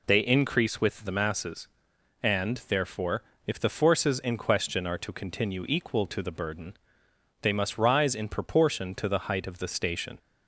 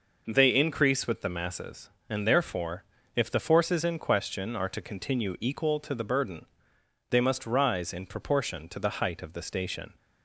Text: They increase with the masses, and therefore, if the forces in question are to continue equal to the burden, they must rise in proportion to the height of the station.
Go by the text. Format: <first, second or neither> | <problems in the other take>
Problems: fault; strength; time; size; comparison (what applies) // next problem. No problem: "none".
neither | none